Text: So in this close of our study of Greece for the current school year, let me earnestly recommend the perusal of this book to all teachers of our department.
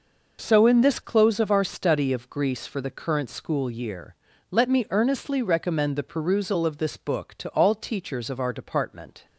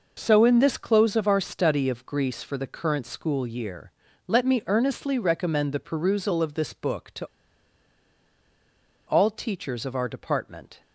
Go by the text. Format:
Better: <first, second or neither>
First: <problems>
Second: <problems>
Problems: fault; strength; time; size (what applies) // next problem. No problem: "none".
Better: first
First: none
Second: pauses between "to" and "all"; strong; at 7.2 s; 1.8 s long